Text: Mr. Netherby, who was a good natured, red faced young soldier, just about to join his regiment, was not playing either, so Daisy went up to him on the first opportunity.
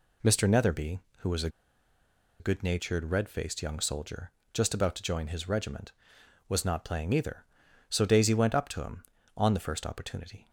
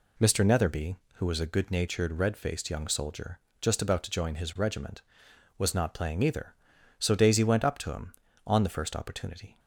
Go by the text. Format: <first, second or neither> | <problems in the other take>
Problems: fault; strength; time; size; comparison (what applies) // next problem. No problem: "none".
second | pauses between "a" and "good"; noticeable; at 1.4 s; 0.91 s long